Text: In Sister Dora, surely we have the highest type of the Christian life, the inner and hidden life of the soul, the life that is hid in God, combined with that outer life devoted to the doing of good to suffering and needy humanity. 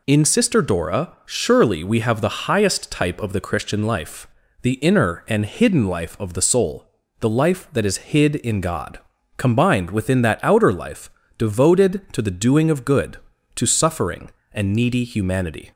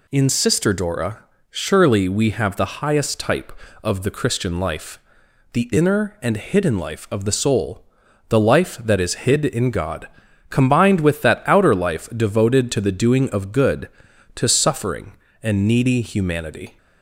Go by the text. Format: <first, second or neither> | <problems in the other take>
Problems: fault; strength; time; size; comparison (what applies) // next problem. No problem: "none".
second | says "within" for "with"; at 9.9 s // pauses between "life" and "devoted"; slight; at 11.0 s; 0.28 s long